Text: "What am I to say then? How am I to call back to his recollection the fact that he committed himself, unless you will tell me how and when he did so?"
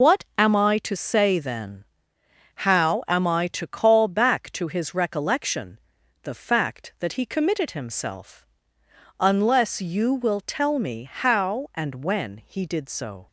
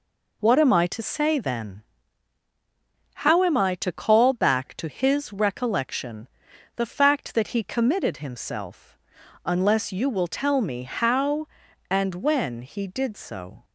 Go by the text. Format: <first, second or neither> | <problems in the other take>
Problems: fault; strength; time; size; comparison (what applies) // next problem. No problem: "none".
second | loses the start of "What"; at 0.0 s; 75 ms // pauses between "recollection" and "the"; at 5.7 s; 0.44 s long; noticeable in the second